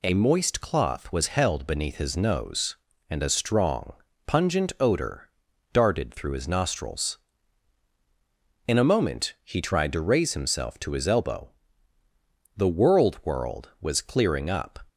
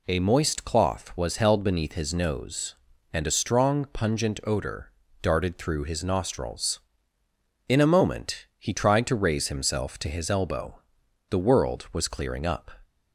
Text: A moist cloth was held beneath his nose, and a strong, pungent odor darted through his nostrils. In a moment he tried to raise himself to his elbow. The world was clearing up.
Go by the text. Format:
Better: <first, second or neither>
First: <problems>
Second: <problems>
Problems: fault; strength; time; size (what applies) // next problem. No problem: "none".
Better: second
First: pauses between "odor" and "darted"; at 5.2 s; 0.44 s long // says "world" twice; at 13.2 s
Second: pauses between "odor" and "darted"; slight; at 4.9 s; 0.30 s long